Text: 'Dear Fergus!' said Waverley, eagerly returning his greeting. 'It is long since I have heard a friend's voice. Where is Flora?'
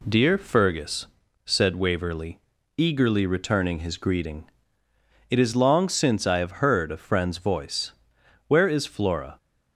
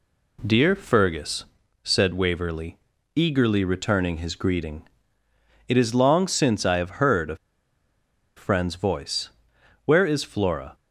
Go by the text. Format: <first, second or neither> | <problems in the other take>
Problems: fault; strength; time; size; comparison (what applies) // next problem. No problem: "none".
first | pauses between "a" and "friend's"; at 7.3 s; 1.0 s long